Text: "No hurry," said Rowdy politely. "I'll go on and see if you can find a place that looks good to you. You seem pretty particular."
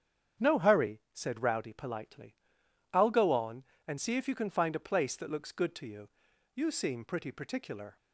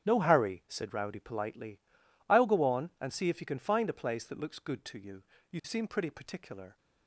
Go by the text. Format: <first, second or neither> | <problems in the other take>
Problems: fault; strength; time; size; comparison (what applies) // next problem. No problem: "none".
neither | starts louder than the rest; strong; the same in both